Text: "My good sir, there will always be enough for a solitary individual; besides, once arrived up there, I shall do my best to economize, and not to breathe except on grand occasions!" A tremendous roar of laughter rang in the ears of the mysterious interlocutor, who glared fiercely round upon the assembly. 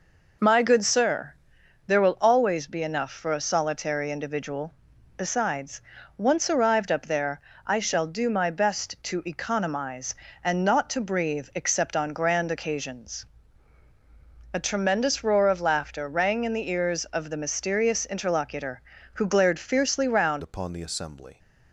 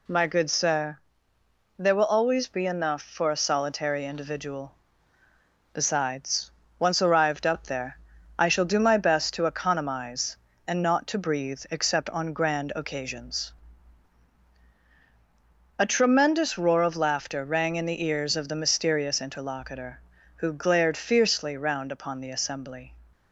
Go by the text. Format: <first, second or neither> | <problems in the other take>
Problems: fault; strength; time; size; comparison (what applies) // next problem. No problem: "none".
second | changes voice at "upon"; from 20.4 s on; 0.9 s long